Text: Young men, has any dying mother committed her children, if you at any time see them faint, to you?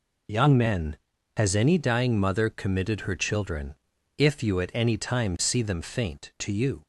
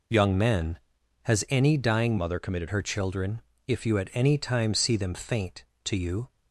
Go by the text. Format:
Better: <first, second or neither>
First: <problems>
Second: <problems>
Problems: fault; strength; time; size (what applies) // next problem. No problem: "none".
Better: first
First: none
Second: changes voice from "mother" to "committed"; from 2.1 to 2.6 s; 0.5 s long